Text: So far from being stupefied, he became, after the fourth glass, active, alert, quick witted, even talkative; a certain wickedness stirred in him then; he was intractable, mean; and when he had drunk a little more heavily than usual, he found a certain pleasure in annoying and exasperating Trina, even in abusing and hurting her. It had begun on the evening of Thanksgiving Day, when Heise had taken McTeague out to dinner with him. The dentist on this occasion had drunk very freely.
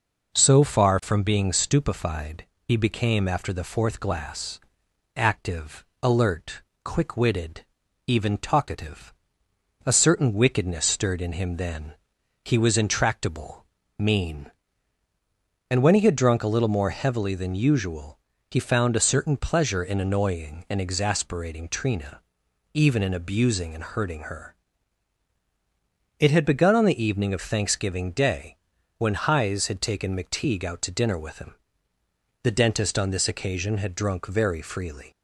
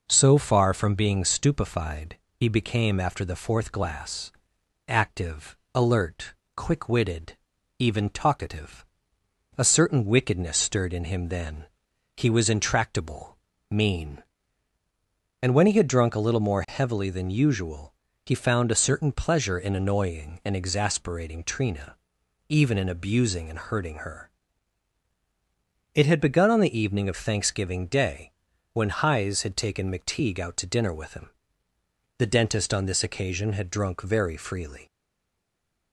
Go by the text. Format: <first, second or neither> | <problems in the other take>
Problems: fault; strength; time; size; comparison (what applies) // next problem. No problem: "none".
first | stays silent after the last word; from 34.8 s on; 1.1 s long